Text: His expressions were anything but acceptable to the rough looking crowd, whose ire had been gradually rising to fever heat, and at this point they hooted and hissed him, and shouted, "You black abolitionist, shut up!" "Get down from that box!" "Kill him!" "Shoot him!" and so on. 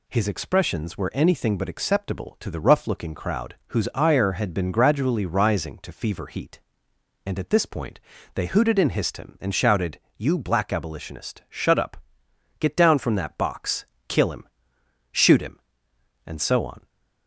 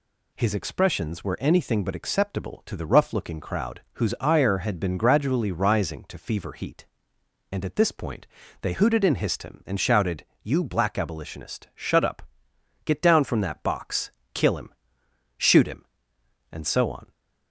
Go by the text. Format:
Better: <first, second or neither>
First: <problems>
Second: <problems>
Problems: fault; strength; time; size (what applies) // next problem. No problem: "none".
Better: neither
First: pauses between "point" and "they"; slight; at 7.9 s; 0.36 s long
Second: pauses between "point" and "they"; slight; at 8.2 s; 0.36 s long